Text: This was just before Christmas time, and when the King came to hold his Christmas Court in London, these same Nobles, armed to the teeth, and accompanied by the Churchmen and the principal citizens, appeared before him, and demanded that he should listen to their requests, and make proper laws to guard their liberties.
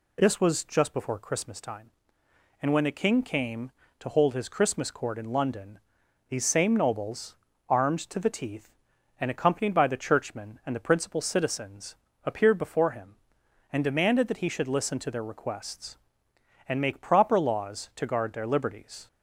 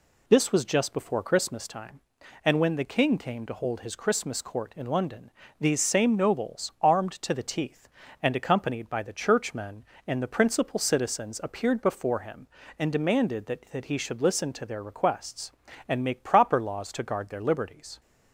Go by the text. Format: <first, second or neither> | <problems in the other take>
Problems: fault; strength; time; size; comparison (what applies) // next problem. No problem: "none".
first | says "that" twice; at 13.6 s